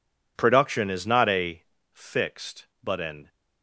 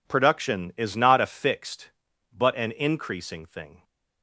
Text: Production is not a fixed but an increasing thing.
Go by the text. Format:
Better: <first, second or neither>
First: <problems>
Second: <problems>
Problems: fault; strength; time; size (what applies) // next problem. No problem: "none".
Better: second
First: pauses between "a" and "fixed"; slight; at 1.6 s; 0.32 s long // stops before "increasing thing"; at 3.2 s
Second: none